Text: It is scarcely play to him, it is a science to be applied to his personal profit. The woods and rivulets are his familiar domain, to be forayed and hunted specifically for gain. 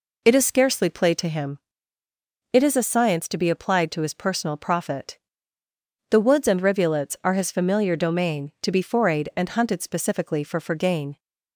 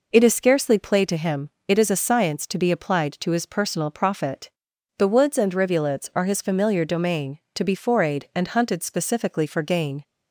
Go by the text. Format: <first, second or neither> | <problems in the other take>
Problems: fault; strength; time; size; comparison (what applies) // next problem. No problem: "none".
second | says "for" twice; at 10.5 s